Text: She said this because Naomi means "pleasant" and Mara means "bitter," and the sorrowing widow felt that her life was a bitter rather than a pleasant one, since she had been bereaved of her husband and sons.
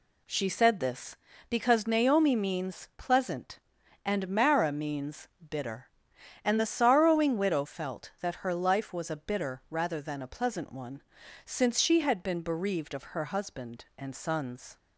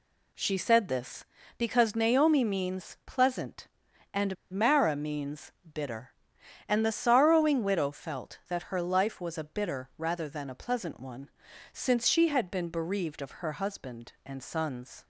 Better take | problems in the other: first | pauses between "and" and "Mara"; slight; at 4.3 s; 0.16 s long // pauses between "means" and "bitter"; slight; at 5.5 s; 0.22 s long; slight in the first

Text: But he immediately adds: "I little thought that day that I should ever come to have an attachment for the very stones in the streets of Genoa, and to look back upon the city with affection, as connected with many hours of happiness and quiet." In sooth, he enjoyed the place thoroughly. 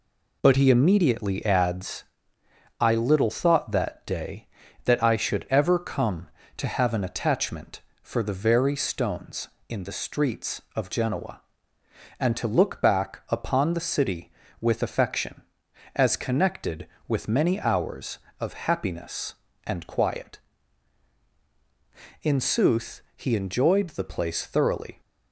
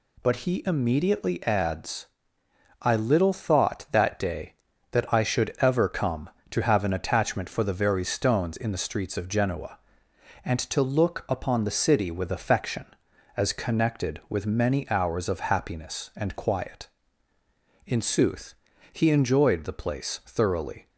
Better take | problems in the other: first | skips "back"; at 11.2 s

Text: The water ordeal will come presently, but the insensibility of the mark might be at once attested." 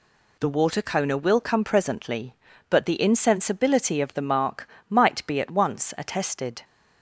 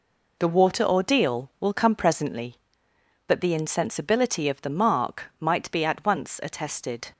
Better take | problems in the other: second | says "coner" for "ordeal"; at 0.8 s // pauses between "mark" and "might"; slight; at 4.6 s; 0.22 s long

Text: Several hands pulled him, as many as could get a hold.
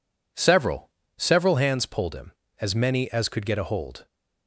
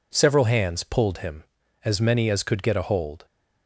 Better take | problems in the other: second | says "Several" twice; at 1.1 s

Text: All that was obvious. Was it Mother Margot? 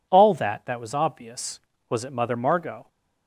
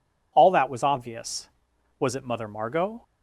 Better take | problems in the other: second | says "that" twice; at 0.6 s

